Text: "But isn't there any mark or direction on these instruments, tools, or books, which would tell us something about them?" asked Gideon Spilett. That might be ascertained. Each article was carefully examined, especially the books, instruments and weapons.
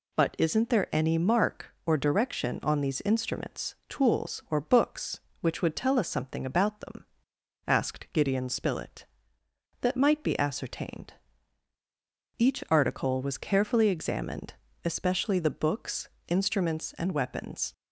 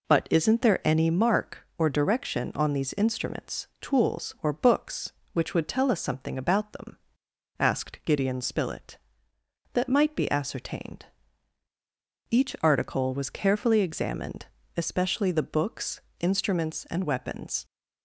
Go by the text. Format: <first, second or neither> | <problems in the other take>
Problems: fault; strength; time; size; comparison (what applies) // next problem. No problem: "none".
first | starts louder than the rest; until 1.2 s; 3.5 dB